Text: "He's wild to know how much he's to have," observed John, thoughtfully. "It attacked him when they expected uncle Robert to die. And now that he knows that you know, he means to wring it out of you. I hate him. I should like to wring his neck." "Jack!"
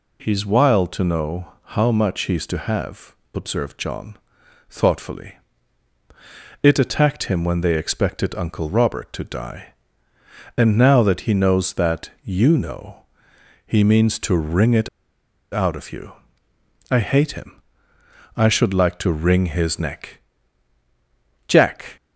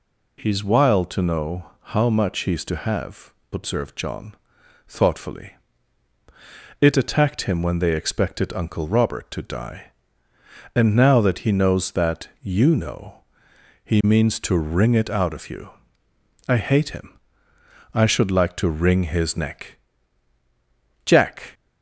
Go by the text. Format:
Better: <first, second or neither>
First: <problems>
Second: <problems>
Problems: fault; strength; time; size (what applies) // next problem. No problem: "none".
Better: second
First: pauses between "know" and "how"; slight; at 1.5 s; 0.22 s long // pauses between "it" and "out"; noticeable; at 14.8 s; 0.65 s long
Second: pauses between "know" and "how"; slight; at 1.7 s; 0.22 s long